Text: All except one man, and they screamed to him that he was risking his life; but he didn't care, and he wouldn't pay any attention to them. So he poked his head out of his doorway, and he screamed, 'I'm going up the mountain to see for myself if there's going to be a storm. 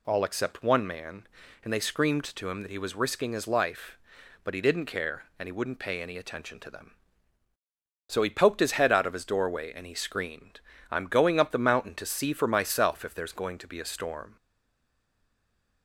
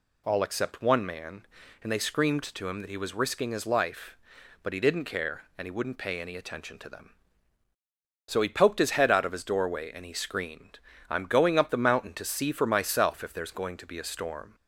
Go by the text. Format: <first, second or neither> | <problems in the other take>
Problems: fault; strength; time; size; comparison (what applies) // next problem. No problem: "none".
second | stays silent after the last word; noticeable; from 14.3 s on; 1.5 s long